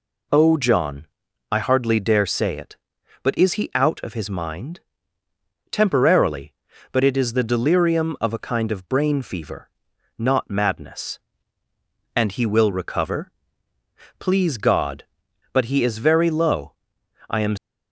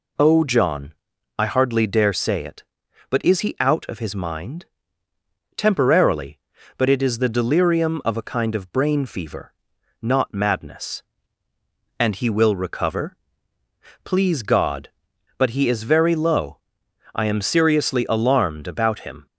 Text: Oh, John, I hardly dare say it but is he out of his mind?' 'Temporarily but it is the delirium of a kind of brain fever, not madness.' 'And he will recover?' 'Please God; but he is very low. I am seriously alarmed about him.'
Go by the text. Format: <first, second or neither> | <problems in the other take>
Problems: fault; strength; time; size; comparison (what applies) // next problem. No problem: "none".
second | stops before "seriously alarmed about him"; at 17.5 s